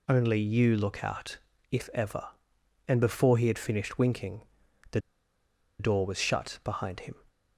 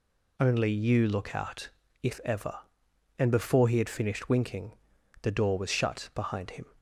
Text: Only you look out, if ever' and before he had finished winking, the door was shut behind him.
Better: second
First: pauses between "the" and "door"; noticeable; at 4.9 s; 0.80 s long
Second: none

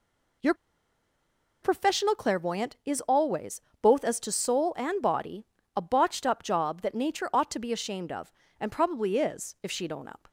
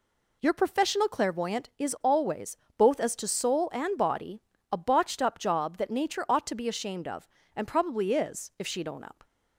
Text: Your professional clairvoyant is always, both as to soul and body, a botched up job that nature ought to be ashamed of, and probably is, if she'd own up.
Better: second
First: pauses between "Your" and "professional"; at 0.5 s; 1.0 s long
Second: none

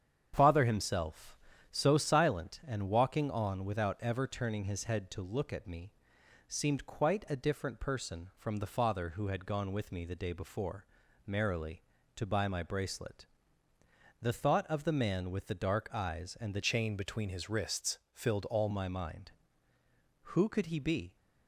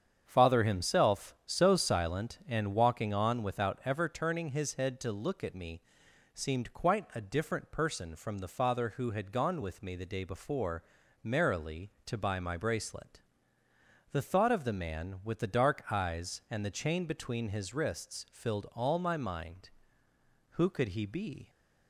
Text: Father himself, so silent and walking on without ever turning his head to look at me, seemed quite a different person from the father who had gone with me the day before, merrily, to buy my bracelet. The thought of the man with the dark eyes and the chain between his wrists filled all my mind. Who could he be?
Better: second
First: starts louder than the rest; strong; until 1.3 s; 8 dB // changes voice from "chain" to "all"; from 16.6 to 18.6 s; 2.0 s long // pauses between "wrists" and "filled"; slight; at 17.9 s; 0.16 s long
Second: starts louder than the rest; strong; until 1.2 s; 8 dB

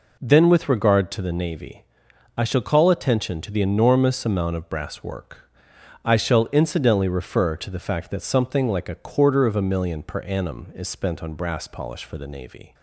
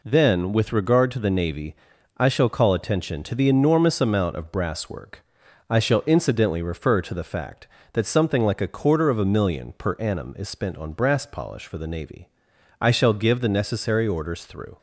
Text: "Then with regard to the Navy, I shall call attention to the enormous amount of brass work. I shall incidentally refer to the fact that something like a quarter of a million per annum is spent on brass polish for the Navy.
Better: first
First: none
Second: goes on to say "I shall give the necessary orders through"; strong; from 12.7 s on; 1.9 s long

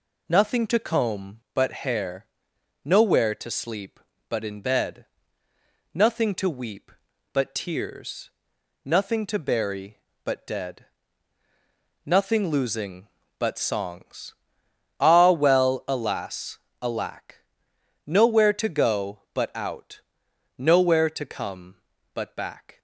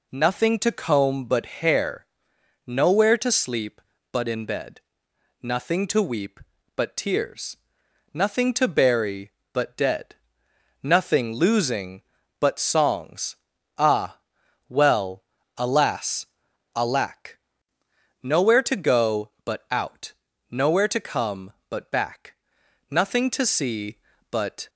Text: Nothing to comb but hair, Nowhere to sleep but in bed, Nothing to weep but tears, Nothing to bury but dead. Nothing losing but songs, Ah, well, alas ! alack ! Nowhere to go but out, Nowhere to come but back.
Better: first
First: none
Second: goes on to say "Nothing to see but"; strong; from 22.4 s on; 2.2 s long

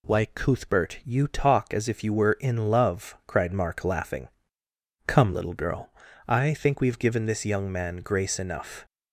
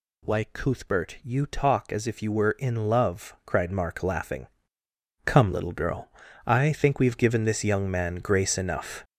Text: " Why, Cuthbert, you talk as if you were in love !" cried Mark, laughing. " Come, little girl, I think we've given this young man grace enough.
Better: first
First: none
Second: gets louder; strong; throughout; 7.5 dB

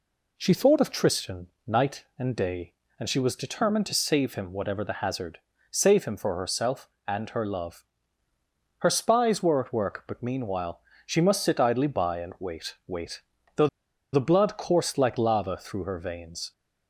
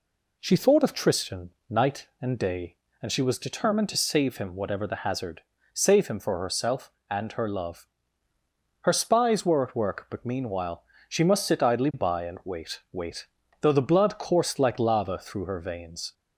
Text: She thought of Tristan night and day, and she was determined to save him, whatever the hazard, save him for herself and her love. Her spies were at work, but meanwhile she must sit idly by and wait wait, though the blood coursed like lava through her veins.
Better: second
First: pauses between "Tristan" and "night"; slight; at 1.4 s; 0.18 s long // pauses between "meanwhile" and "she"; slight; at 10.7 s; 0.26 s long // pauses between "though" and "the"; at 13.6 s; 0.45 s long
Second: pauses between "Tristan" and "night"; slight; at 1.5 s; 0.18 s long // pauses between "meanwhile" and "she"; slight; at 10.8 s; 0.26 s long

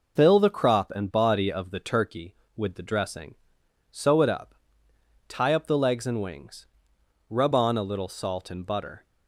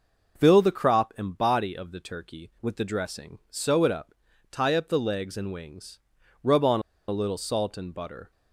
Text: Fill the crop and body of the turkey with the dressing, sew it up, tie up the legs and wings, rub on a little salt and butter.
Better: first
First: none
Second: pauses between "a" and "little"; slight; at 6.8 s; 0.28 s long

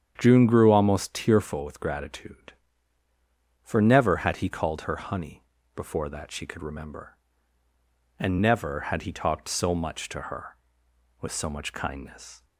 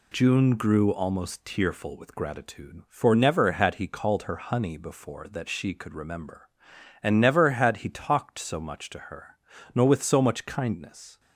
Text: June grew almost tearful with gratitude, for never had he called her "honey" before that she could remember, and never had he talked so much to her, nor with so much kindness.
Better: second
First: starts louder than the rest; strong; until 1.1 s; 8.5 dB // pauses between "honey" and "before"; slight; at 5.4 s; 0.32 s long // skips "nor"; at 10.8 s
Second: none

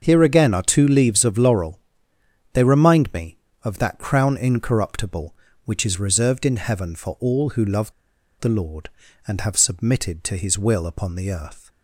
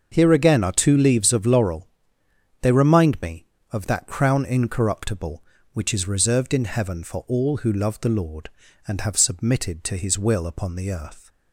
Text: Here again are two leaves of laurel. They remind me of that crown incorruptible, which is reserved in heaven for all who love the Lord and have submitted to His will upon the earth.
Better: second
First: starts louder than the rest; until 1.0 s; 6.5 dB // pauses between "love" and "the"; noticeable; at 7.9 s; 0.48 s long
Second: starts louder than the rest; until 1.1 s; 6.5 dB

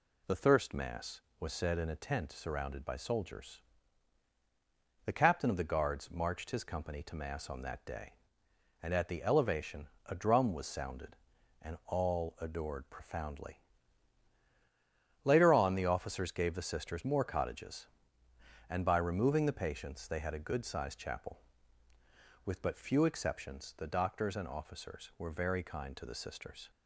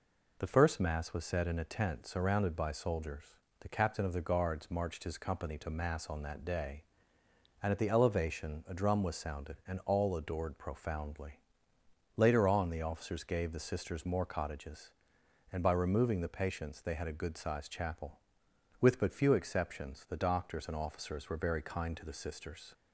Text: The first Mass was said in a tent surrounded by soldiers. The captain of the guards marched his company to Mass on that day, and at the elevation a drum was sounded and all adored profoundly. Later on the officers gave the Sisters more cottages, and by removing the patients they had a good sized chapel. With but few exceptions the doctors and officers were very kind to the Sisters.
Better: second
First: says "thirst" for "first"; at 0.3 s // pauses between "elevation" and "a"; slight; at 9.8 s; 0.18 s long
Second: none

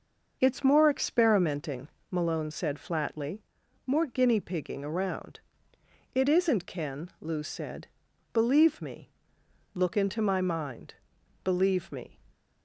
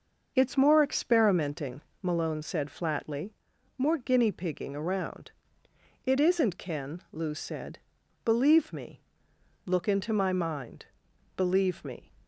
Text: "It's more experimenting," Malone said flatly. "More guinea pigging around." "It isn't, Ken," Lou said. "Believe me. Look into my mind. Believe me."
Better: neither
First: starts louder than the rest; noticeable; until 1.4 s; 6 dB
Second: starts louder than the rest; noticeable; until 1.3 s; 6 dB

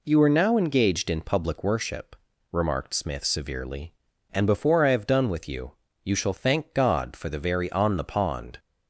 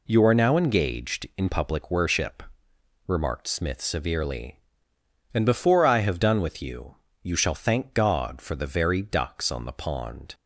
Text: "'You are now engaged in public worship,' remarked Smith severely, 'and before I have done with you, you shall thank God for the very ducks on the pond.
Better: second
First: skips "ducks"; at 7.7 s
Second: none

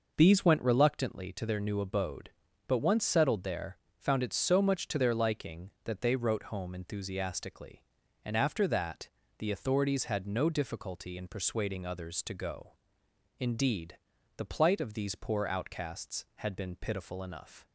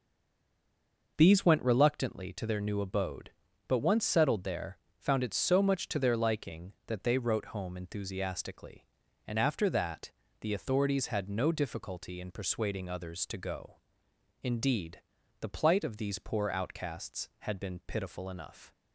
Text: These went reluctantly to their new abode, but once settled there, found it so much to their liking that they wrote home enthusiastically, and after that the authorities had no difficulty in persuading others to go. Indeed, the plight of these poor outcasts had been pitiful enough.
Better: first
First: pauses between "that" and "the"; slight; at 9.0 s; 0.30 s long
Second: stays silent before the first word; until 1.1 s; 1.1 s long // pauses between "that" and "the"; slight; at 10.1 s; 0.30 s long

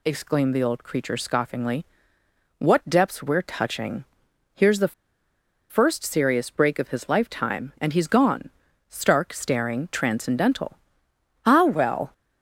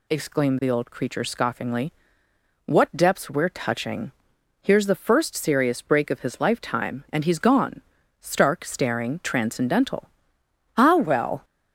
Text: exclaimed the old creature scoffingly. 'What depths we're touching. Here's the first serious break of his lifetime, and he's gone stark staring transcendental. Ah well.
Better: second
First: pauses between "the" and "first"; noticeable; at 4.9 s; 0.76 s long // pauses between "gone" and "stark"; at 8.5 s; 0.38 s long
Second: pauses between "gone" and "stark"; at 7.8 s; 0.38 s long

